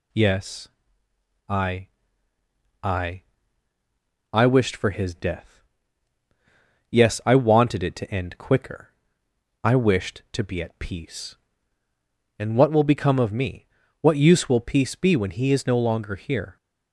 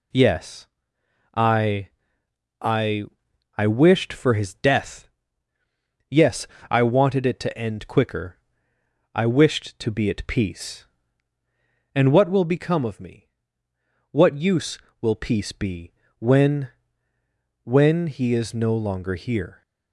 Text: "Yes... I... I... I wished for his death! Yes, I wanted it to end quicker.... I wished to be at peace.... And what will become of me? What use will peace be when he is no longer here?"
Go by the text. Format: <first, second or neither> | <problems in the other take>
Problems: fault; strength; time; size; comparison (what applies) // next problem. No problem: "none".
first | pauses between "be" and "when"; slight; at 15.9 s; 0.28 s long // says "when" twice; at 17.6 s